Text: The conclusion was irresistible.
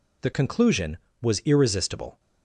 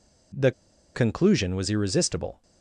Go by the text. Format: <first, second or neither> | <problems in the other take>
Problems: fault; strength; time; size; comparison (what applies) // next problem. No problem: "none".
first | pauses between "The" and "conclusion"; at 0.5 s; 0.43 s long